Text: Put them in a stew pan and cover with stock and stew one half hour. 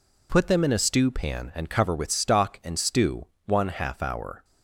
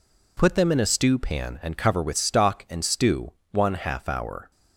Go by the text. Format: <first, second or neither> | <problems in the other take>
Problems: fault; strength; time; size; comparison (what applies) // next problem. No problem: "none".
neither | pauses between "stew" and "one"; slight; the same in both